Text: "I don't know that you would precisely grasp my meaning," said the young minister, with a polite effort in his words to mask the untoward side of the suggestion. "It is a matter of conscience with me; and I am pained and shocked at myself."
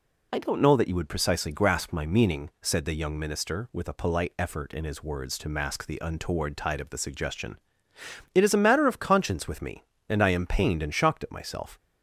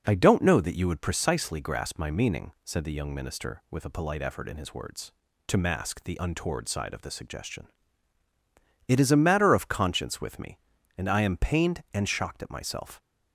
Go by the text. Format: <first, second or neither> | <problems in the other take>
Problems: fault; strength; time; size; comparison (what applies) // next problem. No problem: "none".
second | says "tide" for "side"; at 6.5 s